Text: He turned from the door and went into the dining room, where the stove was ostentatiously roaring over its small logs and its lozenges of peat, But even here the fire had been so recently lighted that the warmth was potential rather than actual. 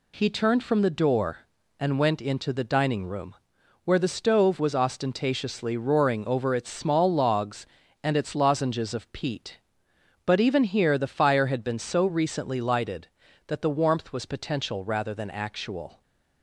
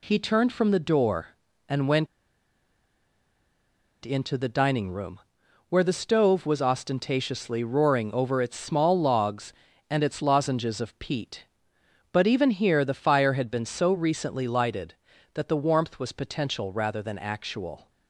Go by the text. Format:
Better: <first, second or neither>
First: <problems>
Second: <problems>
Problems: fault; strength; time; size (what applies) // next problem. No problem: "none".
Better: first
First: none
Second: pauses between "went" and "into"; strong; at 2.0 s; 1.9 s long